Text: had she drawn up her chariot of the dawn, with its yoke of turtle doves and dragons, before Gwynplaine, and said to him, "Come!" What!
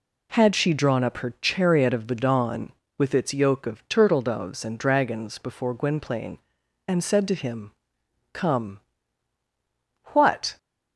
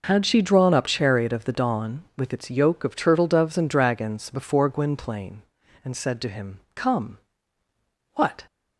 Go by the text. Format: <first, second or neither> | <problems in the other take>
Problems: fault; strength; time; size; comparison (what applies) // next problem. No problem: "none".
first | skips "her"; at 0.8 s